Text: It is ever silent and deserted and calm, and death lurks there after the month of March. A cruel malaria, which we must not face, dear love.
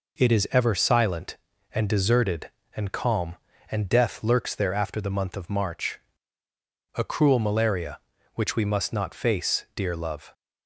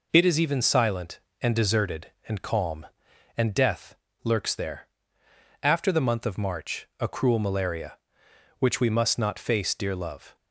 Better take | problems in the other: first | says "even" for "ever"; at 0.3 s // pauses between "death" and "lurks"; slight; at 3.9 s; 0.28 s long // pauses between "there" and "after"; noticeable; at 4.8 s; 0.74 s long

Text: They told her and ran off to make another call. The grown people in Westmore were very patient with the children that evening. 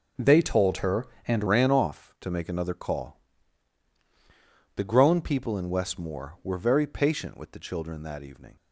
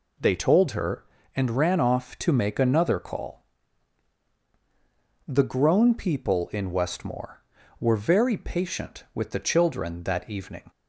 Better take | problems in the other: second | changes voice at "ran"; from 1.4 s on; 7.1 s long

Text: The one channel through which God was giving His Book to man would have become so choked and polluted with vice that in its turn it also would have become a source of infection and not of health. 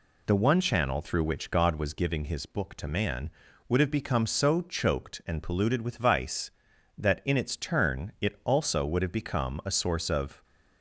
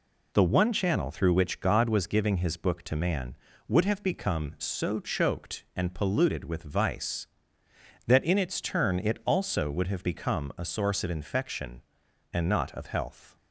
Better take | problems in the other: second | stops before "infection and not of health"; at 10.4 s

